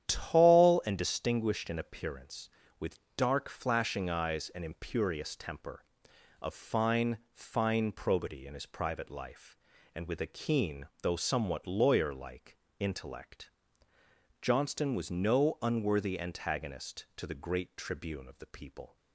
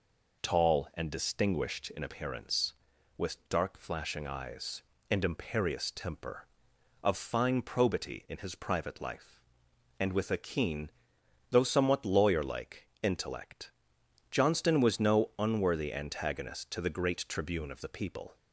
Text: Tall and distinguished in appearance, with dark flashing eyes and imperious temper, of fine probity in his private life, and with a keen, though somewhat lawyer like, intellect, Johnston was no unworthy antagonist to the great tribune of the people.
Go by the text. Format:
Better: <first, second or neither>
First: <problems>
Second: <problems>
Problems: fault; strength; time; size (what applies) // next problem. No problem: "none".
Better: second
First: starts louder than the rest; strong; until 1.1 s; 10 dB // pauses between "with" and "dark"; slight; at 2.9 s; 0.16 s long // says "fine" twice; at 7.3 s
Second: none